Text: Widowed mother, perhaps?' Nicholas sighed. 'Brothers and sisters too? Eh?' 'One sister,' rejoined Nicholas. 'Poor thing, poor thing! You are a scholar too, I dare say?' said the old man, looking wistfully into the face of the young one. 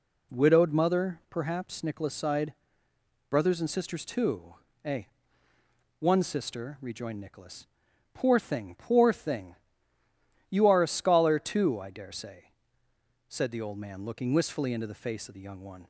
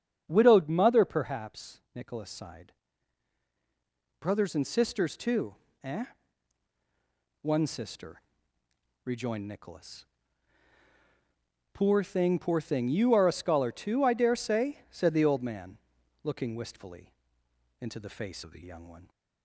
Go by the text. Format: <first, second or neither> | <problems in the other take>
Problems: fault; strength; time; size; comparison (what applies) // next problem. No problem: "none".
first | starts louder than the rest; strong; until 1.2 s; 7.5 dB // pauses between "wistfully" and "into"; noticeable; at 17.1 s; 0.68 s long // changes voice from "of" to "the"; from 18.4 to 18.6 s; 0.2 s long